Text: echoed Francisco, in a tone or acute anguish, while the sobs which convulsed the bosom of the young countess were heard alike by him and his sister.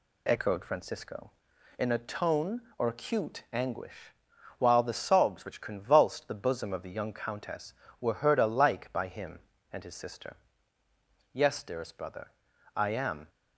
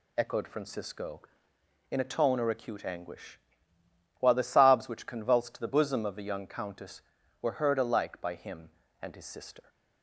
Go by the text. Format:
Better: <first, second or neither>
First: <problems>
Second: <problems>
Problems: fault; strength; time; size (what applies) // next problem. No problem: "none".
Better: second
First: goes on to say "Yes dearest brother I am"; strong; from 11.3 s on; 1.9 s long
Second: none